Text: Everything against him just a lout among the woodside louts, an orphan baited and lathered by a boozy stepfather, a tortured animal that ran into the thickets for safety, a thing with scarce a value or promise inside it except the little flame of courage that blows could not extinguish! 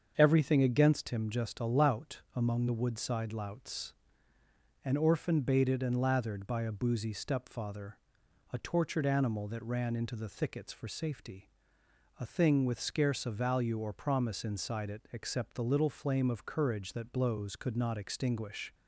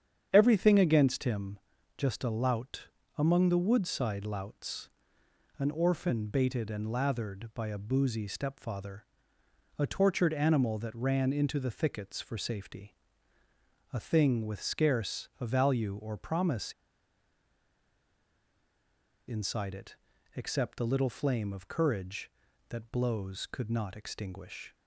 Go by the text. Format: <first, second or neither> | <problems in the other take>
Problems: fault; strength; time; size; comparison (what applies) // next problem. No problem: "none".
first | starts louder than the rest; strong; until 1.3 s; 8.5 dB; also in the first // pauses between "him" and "just"; at 1.5 s; 0.38 s long // pauses between "lout" and "among"; slight; at 2.8 s; 0.28 s long // pauses between "promise" and "inside"; strong; at 16.7 s; 2.5 s long // pauses between "it" and "except"; at 19.9 s; 0.40 s long